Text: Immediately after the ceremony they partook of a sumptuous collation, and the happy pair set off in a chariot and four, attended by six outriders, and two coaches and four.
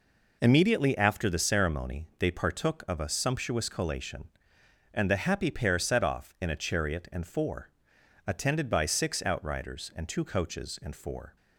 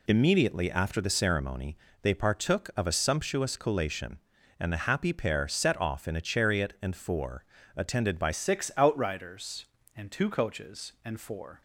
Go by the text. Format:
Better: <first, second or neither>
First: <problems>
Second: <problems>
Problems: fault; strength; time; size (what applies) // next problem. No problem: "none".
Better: first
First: none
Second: pauses between "ceremony" and "they"; slight; at 1.7 s; 0.26 s long // changes voice at "six"; from 8.3 s on; 3.3 s long